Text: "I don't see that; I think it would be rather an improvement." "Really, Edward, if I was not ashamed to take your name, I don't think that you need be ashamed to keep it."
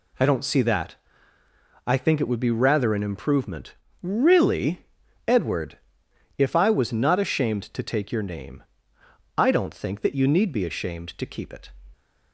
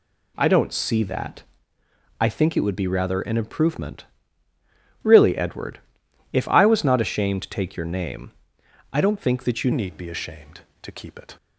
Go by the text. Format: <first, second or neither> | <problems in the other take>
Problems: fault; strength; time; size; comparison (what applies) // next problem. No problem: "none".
first | changes voice at "need"; from 9.7 s on; 1.6 s long